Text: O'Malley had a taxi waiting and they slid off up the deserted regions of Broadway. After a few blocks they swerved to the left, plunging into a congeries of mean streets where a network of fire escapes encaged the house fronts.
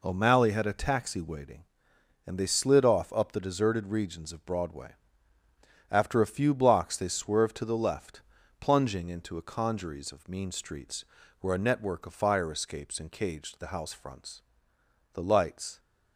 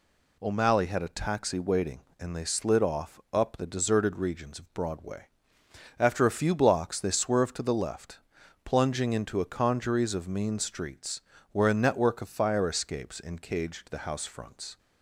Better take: second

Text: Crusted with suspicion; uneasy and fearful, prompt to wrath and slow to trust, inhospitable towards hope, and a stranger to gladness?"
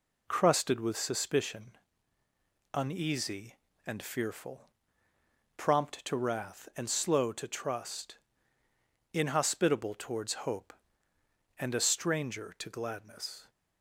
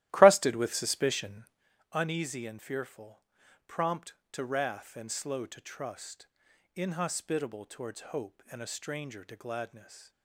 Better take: first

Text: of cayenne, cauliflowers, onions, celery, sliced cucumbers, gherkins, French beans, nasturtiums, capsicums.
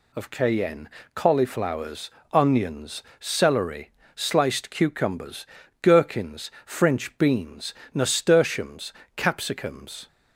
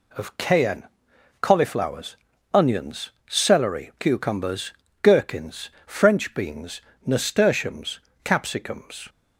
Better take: first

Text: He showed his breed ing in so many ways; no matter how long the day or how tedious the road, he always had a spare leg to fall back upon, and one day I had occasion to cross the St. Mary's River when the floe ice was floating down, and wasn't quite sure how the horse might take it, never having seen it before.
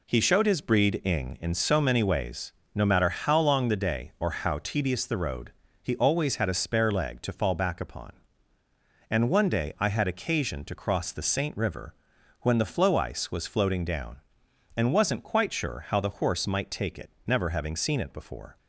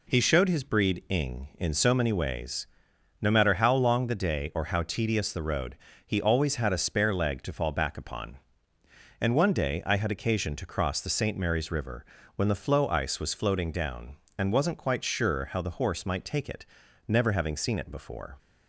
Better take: second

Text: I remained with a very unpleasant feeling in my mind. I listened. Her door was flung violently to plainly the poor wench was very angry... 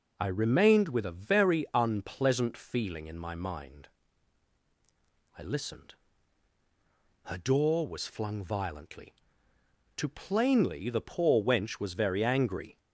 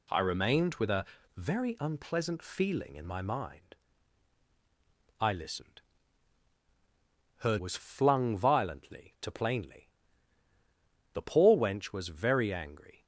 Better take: first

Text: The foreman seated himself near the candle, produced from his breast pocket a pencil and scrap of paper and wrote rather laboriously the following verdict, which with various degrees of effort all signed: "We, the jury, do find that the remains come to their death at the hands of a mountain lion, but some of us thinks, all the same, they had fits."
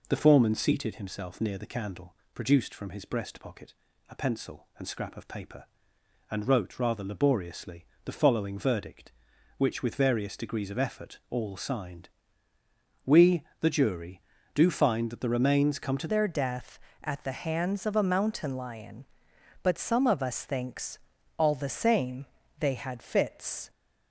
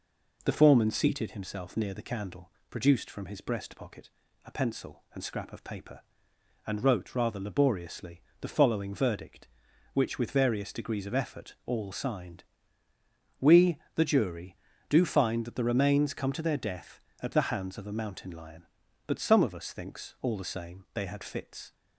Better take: second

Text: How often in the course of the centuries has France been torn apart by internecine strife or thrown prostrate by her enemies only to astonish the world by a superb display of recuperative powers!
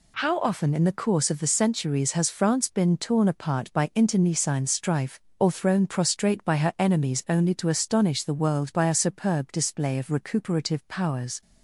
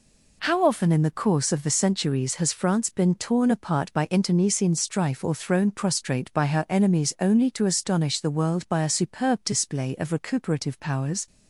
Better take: neither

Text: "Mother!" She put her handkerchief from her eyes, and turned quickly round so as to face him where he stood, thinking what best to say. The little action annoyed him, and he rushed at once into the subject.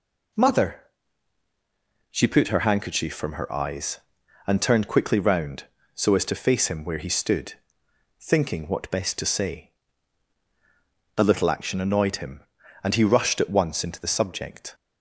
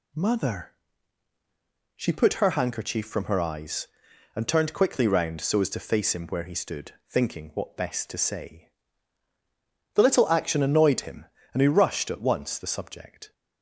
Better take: first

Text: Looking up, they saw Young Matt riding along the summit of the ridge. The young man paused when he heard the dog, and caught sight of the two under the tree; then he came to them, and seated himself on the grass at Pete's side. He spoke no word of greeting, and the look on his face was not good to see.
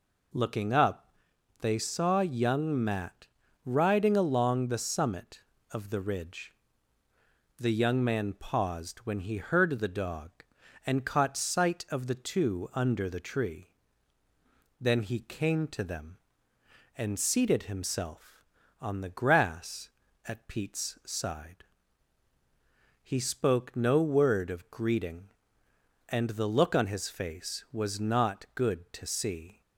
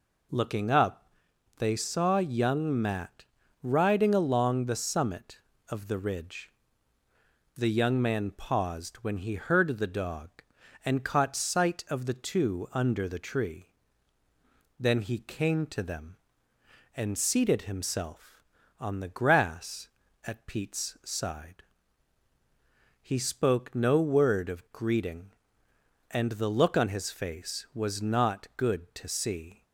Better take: neither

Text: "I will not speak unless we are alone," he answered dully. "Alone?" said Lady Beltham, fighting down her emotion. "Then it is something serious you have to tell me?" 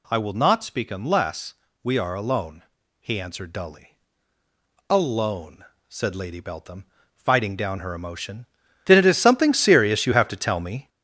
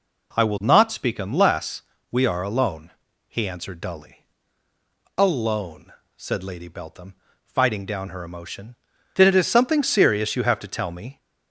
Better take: second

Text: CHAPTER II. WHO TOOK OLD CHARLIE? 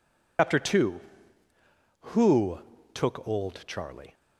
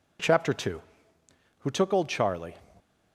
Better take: second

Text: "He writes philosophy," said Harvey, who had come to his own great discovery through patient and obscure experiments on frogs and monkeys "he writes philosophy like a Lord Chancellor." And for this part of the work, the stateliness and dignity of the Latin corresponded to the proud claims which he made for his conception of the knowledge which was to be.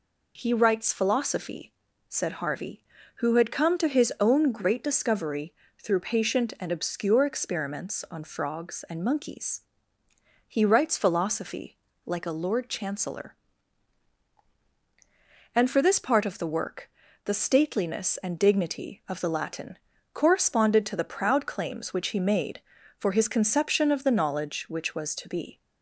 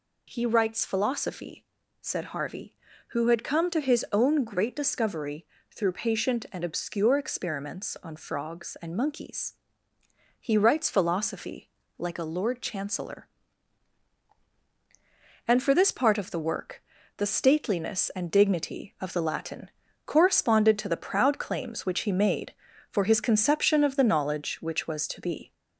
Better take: first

